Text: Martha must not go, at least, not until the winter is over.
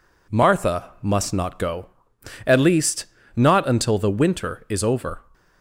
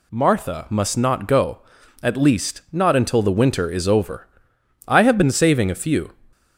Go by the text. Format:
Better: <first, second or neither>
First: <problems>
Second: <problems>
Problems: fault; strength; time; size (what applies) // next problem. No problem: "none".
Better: first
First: none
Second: goes on to say "I have been saving a few"; noticeable; from 4.8 s on; 1.2 s long